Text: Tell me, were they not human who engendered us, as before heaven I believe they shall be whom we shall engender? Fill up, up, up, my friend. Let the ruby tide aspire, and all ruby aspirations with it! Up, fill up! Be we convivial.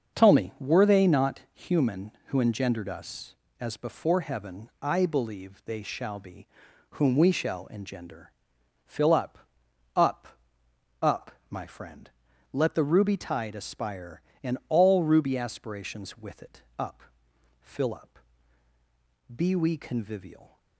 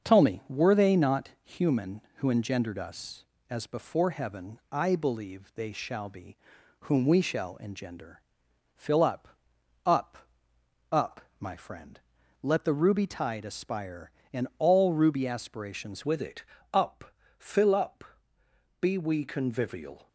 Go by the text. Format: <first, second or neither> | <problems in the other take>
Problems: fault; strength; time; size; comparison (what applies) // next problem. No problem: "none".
first | starts louder than the rest; until 1.1 s; 6.5 dB; also in the first // pauses between "be" and "whom"; noticeable; at 6.3 s; 0.46 s long; noticeable in the first // changes voice at "with"; from 16.0 s on; 4.0 s long